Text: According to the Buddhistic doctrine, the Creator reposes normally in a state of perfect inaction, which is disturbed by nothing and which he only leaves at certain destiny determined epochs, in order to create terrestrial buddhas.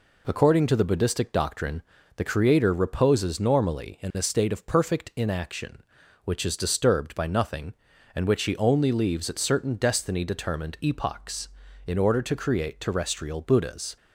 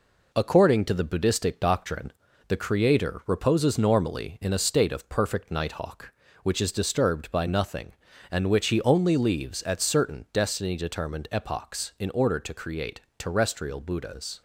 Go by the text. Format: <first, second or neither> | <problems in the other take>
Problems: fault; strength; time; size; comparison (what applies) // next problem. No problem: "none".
first | says "nighthawk" for "inaction"; at 5.5 s // pauses between "create" and "terrestrial"; slight; at 13.0 s; 0.18 s long